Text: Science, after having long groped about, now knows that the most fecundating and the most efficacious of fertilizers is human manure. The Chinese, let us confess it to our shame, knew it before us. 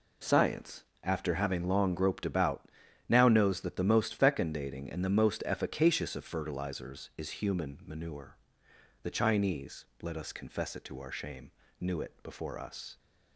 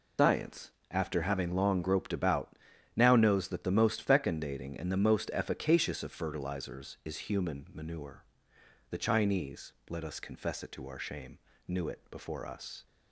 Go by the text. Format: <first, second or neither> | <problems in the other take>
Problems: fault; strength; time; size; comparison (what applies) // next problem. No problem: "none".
first | loses the start of "Science"; at 0.1 s; 105 ms